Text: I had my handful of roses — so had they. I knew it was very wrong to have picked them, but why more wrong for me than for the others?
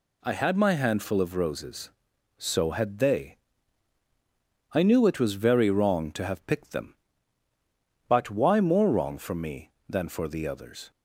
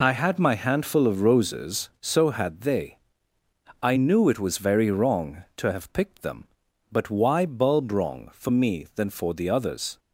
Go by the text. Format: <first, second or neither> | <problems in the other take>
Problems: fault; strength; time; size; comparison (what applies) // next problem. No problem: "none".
first | says "bulb" for "more"; at 7.4 s